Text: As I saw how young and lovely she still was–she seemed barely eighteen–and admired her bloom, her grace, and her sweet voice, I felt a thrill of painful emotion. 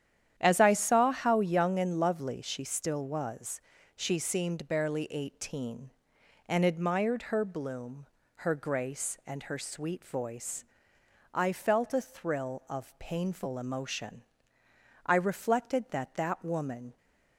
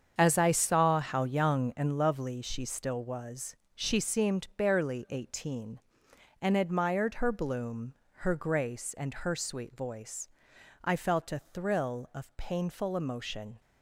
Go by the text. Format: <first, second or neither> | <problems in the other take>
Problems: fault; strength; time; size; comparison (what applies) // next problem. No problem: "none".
second | starts louder than the rest; strong; until 1.3 s; 10 dB; strong in the second // goes on to say "I reflected that that woman"; strong; from 15.0 s on; 1.9 s long